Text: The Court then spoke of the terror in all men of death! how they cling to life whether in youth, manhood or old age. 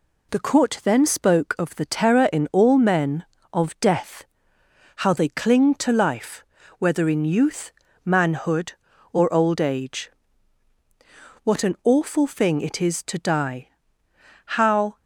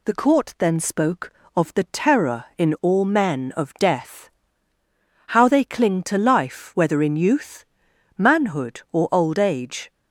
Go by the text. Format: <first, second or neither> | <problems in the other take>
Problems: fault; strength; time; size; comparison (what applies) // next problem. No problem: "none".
second | pauses between "life" and "whether"; slight; at 6.4 s; 0.34 s long // goes on to say "What an awful thing it is to die how"; strong; from 11.4 s on; 3.5 s long